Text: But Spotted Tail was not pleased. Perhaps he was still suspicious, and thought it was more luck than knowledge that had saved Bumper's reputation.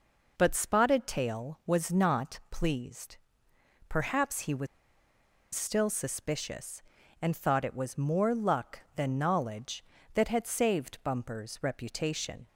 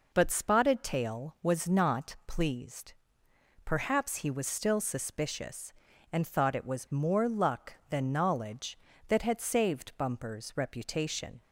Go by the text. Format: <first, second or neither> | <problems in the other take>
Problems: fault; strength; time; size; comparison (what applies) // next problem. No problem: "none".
second | pauses between "was" and "still"; noticeable; at 4.6 s; 0.88 s long